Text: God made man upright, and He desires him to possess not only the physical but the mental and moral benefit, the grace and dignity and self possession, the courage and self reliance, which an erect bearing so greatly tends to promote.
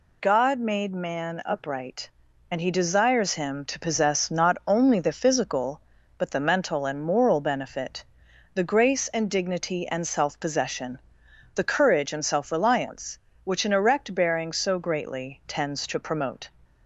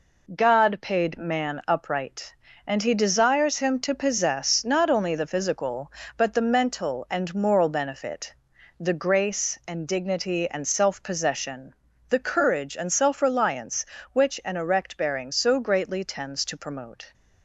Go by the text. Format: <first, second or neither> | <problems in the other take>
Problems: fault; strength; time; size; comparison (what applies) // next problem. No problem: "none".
first | says "paid" for "made"; at 0.8 s